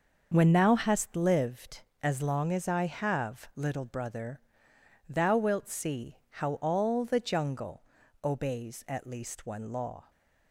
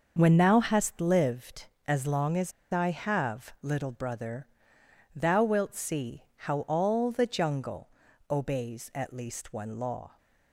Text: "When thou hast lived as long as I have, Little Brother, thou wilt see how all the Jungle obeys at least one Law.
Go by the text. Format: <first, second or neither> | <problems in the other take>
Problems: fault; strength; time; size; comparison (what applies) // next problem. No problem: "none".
first | starts louder than the rest; noticeable; until 1.1 s; 6 dB; noticeable in the first // pauses between "as" and "I"; slight; at 2.5 s; 0.20 s long // pauses between "Jungle" and "obeys"; at 7.8 s; 0.40 s long; also in the first